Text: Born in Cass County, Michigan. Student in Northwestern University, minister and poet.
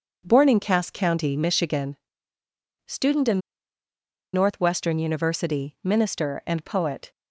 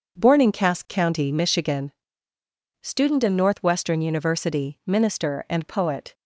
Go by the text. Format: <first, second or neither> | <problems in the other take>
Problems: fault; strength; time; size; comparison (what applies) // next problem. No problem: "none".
second | pauses between "in" and "Northwestern"; noticeable; at 3.4 s; 0.93 s long